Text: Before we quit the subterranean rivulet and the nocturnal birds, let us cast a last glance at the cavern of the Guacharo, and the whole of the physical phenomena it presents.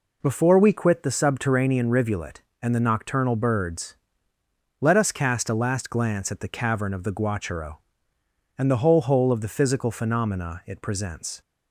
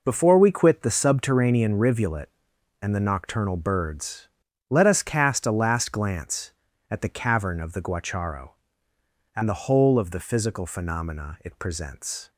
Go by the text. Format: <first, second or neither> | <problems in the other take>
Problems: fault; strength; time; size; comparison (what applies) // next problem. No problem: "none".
second | says "whole" twice; at 9.0 s